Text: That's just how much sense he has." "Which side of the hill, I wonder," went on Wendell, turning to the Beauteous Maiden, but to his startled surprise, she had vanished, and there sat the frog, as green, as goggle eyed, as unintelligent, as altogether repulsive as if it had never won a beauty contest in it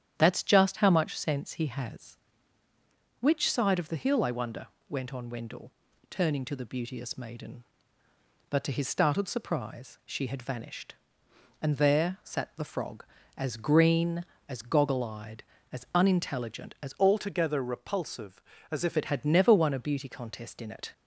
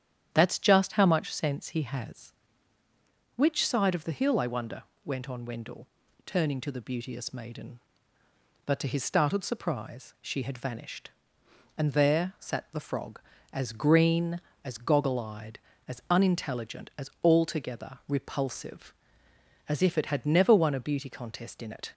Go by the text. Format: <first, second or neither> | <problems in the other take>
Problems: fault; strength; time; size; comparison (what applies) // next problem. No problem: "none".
second | starts louder than the rest; strong; until 1.1 s; 9.5 dB; strong in the second // changes voice from "altogether" to "if"; from 16.9 to 18.9 s; 2.0 s long